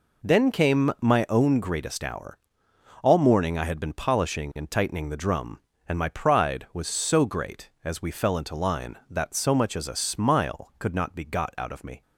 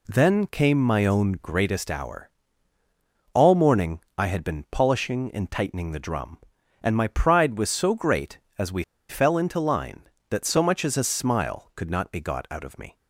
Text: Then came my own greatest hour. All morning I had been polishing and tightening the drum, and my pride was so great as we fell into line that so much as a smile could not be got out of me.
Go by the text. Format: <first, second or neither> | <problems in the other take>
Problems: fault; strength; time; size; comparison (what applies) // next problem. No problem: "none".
first | pauses between "morning" and "I"; slight; at 4.0 s; 0.16 s long // pauses between "we" and "fell"; slight; at 8.8 s; 0.25 s long